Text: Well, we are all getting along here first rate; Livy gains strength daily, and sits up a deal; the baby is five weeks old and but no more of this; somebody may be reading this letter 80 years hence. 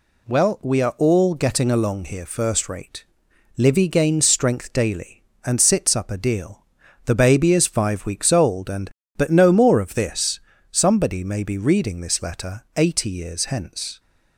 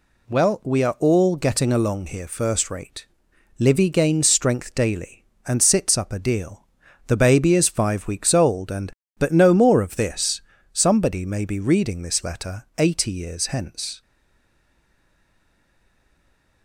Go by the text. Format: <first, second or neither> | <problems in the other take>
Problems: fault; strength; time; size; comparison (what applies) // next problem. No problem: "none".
first | stays silent after the last word; strong; from 14.0 s on; 2.6 s long